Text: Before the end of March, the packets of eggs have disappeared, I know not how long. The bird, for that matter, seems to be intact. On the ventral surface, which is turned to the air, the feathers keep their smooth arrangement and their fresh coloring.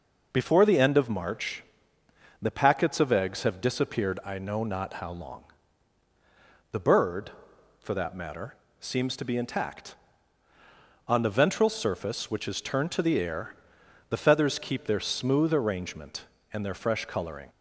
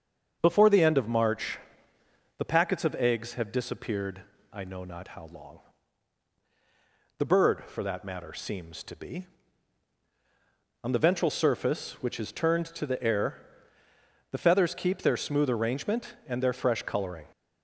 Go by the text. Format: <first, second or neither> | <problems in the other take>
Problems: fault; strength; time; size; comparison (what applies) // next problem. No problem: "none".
first | starts louder than the rest; until 1.4 s; 7 dB // skips "intact"; at 10.0 s